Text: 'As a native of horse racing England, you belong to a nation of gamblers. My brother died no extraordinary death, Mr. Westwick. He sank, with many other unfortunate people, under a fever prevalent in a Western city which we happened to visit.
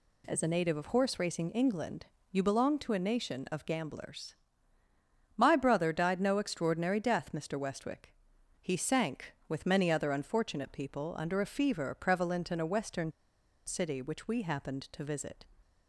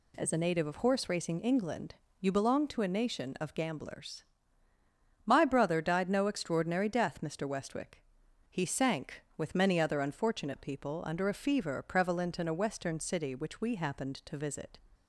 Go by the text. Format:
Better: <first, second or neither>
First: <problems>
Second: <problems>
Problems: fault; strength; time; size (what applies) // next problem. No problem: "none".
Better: second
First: pauses between "Western" and "city"; noticeable; at 13.1 s; 0.55 s long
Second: none